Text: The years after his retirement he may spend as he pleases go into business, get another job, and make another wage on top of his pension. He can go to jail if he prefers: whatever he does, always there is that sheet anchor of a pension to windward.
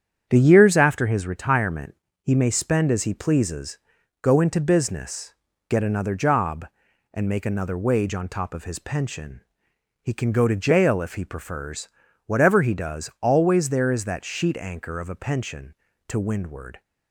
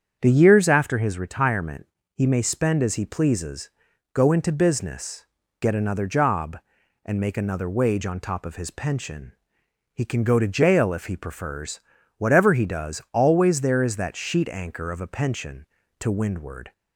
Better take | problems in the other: second | gets quieter; noticeable; throughout; 5.5 dB // starts louder than the rest; strong; until 1.3 s; 8.5 dB; strong in the second // pauses between "retirement" and "he"; slight; at 1.9 s; 0.26 s long; slight in the second // pauses between "pleases" and "go"; at 3.7 s; 0.44 s long; also in the second

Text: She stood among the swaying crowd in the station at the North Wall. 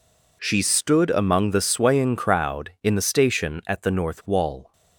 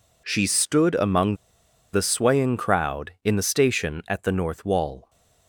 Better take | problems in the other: first | pauses between "among" and "the"; noticeable; at 1.3 s; 0.57 s long

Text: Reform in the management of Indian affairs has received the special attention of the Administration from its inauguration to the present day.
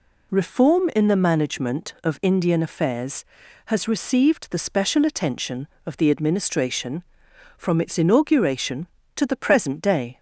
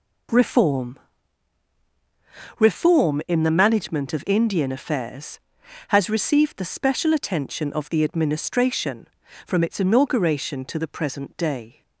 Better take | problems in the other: first | says "Reform" twice; at 2.5 s

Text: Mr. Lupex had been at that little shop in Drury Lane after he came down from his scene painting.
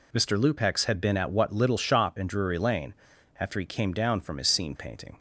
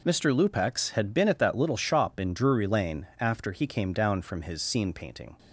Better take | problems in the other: second | says "what" for "that"; at 1.3 s // pauses between "Lane" and "after"; noticeable; at 2.9 s; 0.46 s long

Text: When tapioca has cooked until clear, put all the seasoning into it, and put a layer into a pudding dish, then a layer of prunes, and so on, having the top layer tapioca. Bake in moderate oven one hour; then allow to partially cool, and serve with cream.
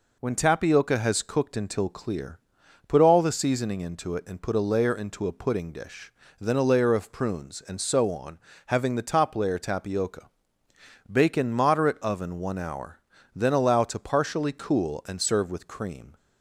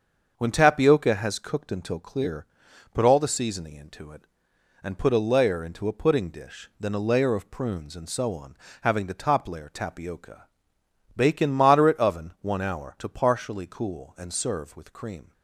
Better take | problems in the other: first | starts louder than the rest; until 1.3 s; 7 dB // skips "then allow"; at 12.9 s

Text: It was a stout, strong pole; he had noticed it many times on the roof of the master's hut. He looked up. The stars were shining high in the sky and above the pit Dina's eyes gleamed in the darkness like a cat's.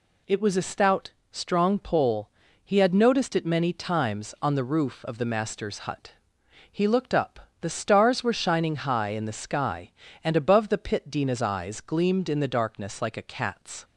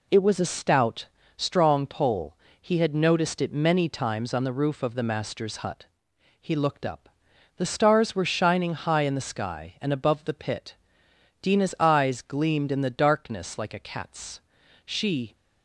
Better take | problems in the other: first | pauses between "pit" and "Dina's"; noticeable; at 10.7 s; 0.66 s long // goes on to say "She"; slight; from 14.8 s on; 0.48 s long

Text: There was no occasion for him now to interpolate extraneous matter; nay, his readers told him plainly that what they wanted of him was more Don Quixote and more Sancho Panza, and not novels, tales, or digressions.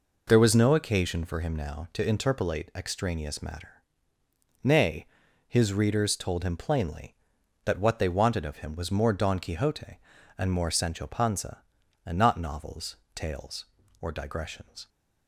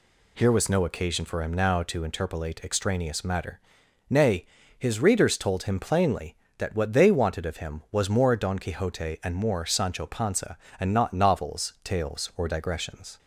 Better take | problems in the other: first | says "Here" for "There"; at 0.3 s

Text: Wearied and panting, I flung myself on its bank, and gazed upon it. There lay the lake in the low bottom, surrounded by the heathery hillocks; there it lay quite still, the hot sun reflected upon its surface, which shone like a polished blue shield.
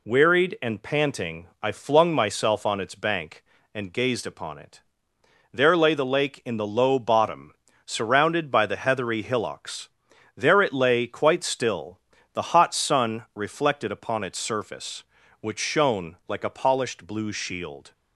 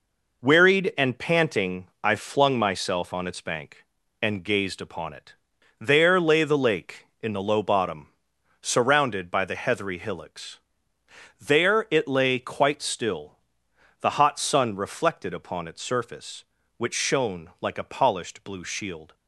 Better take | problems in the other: neither | none

